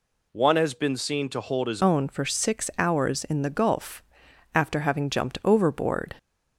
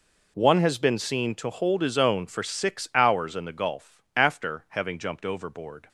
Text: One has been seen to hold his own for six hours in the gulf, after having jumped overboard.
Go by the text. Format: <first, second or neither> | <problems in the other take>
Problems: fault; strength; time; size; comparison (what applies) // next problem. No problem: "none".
second | changes voice at "own"; from 1.8 s on; 4.3 s long